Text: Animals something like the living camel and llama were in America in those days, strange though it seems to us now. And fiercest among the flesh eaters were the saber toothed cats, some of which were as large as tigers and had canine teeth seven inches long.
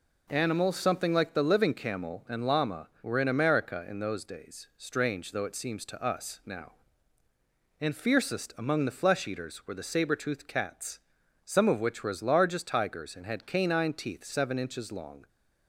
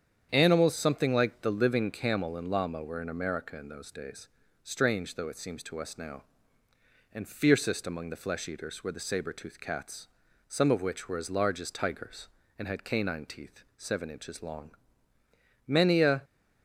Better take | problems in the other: first | starts louder than the rest; strong; until 1.3 s; 8.5 dB // goes on to say "Many a"; from 15.6 s on; 0.54 s long

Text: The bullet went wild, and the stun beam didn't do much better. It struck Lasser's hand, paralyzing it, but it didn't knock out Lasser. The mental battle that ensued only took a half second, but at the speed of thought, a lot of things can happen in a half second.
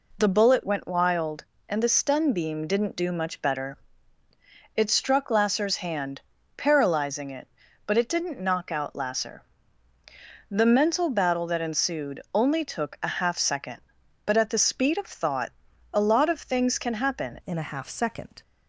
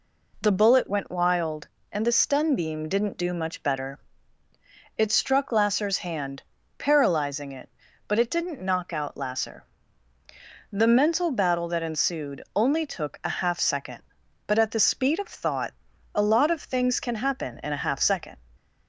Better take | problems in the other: second | changes voice at "in"; from 17.4 s on; 1.0 s long

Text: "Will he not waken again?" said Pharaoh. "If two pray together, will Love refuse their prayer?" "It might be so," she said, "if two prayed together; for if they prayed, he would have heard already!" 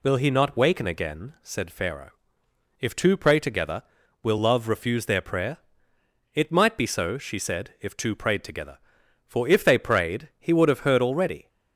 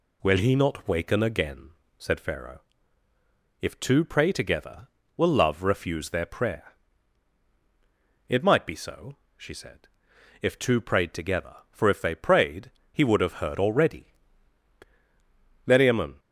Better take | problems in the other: first | goes on to say "Meriamun"; from 15.6 s on; 0.54 s long

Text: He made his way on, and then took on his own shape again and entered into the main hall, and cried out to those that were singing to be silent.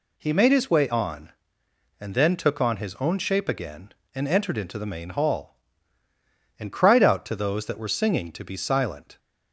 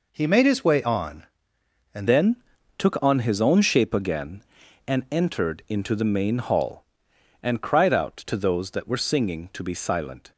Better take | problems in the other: first | changes voice at "then"; from 2.0 s on; 8.3 s long // pauses between "then" and "took"; at 2.3 s; 0.42 s long

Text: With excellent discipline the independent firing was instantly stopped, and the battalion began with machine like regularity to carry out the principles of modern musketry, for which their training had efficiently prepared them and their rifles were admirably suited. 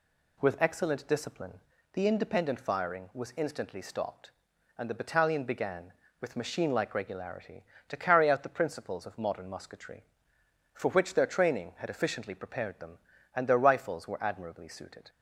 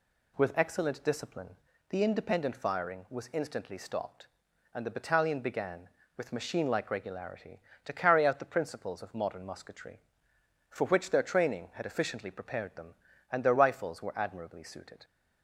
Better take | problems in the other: neither | pauses between "discipline" and "the"; the same in both

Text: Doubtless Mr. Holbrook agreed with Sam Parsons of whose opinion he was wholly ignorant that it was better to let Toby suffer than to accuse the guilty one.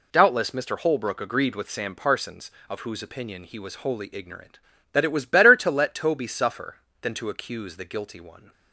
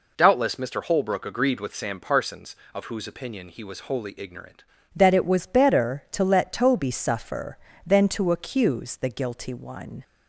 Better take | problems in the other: first | changes voice at "that"; from 4.9 s on; 5.1 s long

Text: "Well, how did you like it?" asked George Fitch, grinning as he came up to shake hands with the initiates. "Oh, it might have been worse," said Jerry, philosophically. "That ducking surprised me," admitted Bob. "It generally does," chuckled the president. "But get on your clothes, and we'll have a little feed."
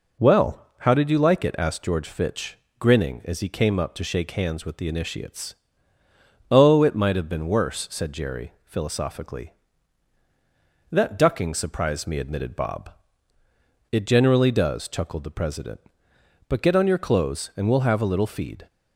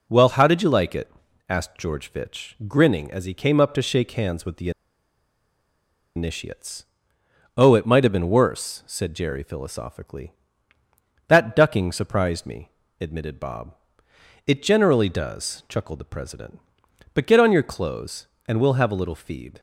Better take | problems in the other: first | pauses between "the" and "initiates"; strong; at 4.7 s; 1.4 s long

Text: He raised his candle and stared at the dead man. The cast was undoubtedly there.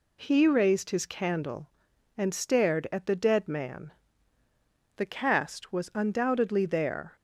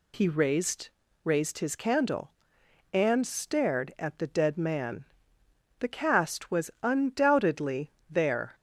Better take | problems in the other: first | says "raised" twice; at 1.2 s // pauses between "undoubtedly" and "there"; slight; at 7.9 s; 0.18 s long

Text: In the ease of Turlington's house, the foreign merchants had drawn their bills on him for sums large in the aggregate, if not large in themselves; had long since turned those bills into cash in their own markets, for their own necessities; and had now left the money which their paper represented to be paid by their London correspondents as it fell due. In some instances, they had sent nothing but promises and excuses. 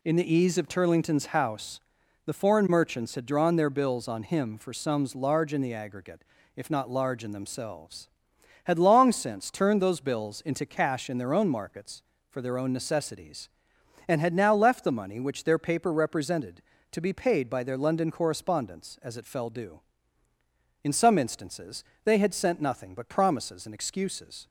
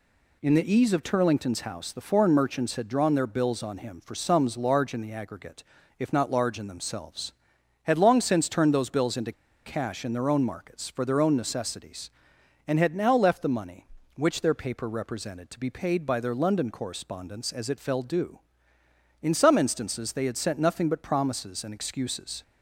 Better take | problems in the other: first | pauses between "into" and "cash"; slight; at 9.3 s; 0.31 s long

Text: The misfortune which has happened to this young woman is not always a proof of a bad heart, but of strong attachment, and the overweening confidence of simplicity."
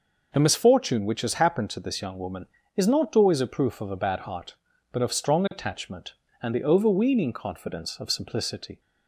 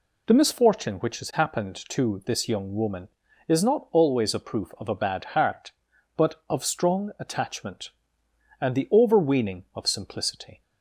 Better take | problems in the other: first | skips "confidence"; at 9.6 s

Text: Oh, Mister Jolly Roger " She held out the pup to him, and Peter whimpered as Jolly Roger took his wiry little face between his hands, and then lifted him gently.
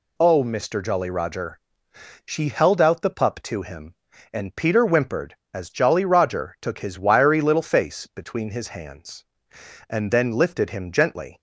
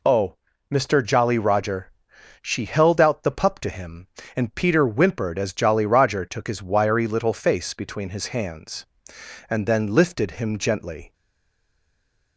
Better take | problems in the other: first | stays silent after the last word; noticeable; from 11.1 s on; 1.2 s long

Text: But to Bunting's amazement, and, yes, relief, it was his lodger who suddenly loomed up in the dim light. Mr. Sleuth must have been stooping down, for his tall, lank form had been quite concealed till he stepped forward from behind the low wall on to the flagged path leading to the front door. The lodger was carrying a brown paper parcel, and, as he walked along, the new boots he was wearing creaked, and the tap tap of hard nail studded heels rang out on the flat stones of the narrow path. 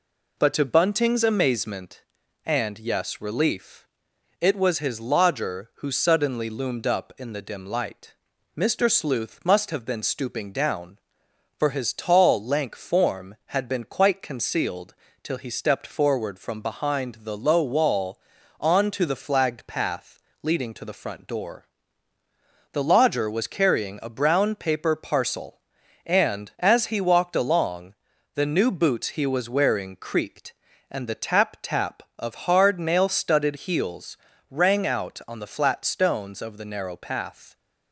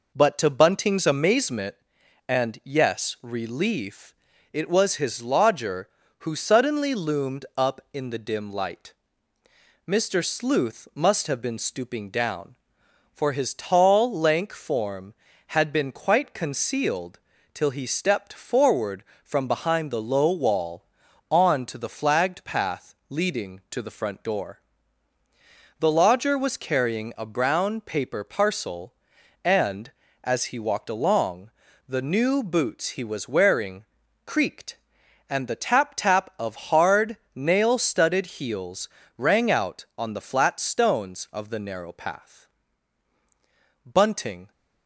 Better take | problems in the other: first | pauses between "concealed" and "till"; slight; at 17.1 s; 0.34 s long; slight in the first // pauses between "path" and "leading"; slight; at 22.9 s; 0.16 s long; slight in the first // pauses between "wearing" and "creaked"; at 33.8 s; 0.40 s long // pauses between "hard" and "nail"; slight; at 37.1 s; 0.18 s long // pauses between "heels" and "rang"; slight; at 38.8 s; 0.30 s long; slight in the first // goes on to say "Bunting"; noticeable; from 43.8 s on; 0.66 s long

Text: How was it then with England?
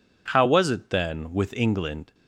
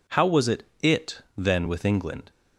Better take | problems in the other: first | says "it" twice; at 0.8 s

